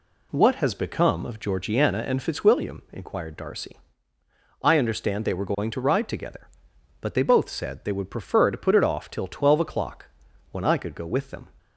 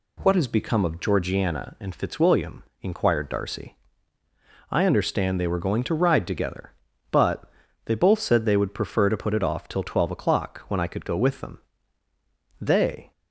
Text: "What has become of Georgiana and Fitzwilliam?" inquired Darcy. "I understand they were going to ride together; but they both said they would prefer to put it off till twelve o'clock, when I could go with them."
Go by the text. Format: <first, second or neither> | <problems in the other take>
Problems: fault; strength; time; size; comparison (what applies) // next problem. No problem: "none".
first | pauses between "but" and "they"; slight; at 7.4 s; 0.36 s long // goes on to say "They"; from 12.5 s on; 0.52 s long